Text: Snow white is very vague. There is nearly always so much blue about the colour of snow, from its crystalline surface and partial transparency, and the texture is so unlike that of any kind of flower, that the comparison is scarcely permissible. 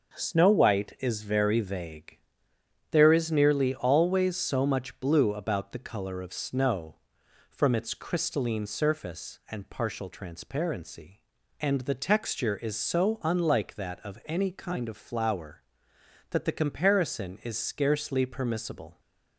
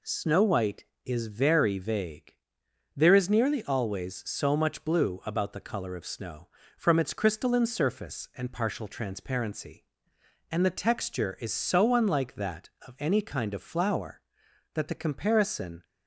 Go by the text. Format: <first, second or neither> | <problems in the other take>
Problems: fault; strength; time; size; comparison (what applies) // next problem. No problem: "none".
first | stops before "is scarcely permissible"; at 15.8 s